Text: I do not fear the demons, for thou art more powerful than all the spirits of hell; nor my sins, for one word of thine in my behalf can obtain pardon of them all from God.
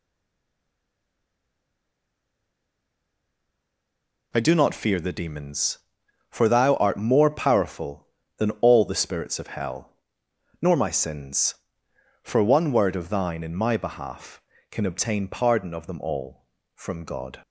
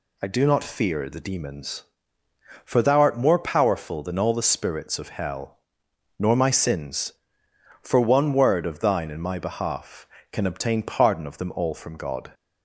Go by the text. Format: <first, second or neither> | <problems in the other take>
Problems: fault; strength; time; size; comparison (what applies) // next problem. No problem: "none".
second | stays silent before the first word; strong; until 4.3 s; 4.3 s long